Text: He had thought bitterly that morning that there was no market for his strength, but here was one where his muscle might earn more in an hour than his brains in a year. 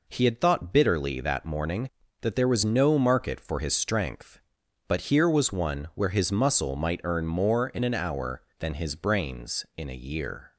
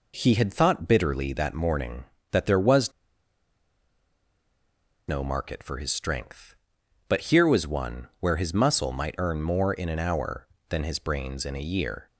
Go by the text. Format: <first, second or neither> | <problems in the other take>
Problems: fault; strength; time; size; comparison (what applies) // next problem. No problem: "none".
first | pauses between "was" and "no"; strong; at 2.9 s; 2.1 s long